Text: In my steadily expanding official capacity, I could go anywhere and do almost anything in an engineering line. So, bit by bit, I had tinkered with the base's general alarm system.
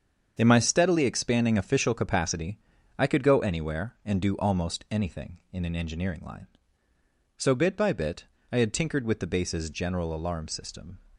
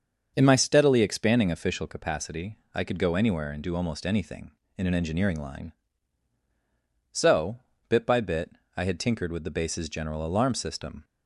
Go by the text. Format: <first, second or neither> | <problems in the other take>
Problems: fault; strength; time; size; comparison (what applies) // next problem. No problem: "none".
neither | starts louder than the rest; the same in both